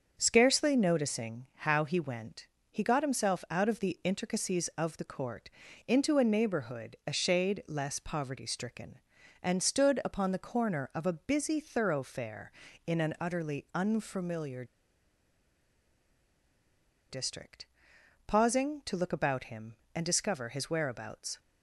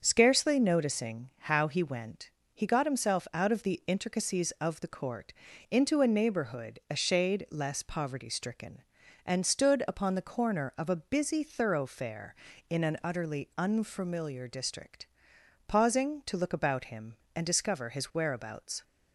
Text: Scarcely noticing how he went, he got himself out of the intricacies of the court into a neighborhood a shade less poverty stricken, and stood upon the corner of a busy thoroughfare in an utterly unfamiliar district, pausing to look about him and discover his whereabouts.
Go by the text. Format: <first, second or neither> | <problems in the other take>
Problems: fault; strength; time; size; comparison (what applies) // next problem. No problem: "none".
second | starts louder than the rest; until 1.2 s; 6.5 dB; also in the second // pauses between "court" and "into"; at 5.4 s; 0.38 s long; also in the second // pauses between "unfamiliar" and "district"; strong; at 14.6 s; 2.4 s long